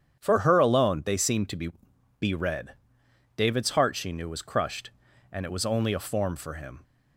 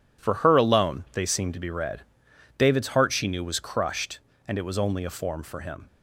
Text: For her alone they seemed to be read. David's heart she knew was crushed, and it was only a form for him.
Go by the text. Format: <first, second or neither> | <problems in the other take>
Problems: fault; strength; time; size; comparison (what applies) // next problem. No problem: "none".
second | starts louder than the rest; strong; until 1.2 s; 8.5 dB // says "be" twice; at 2.1 s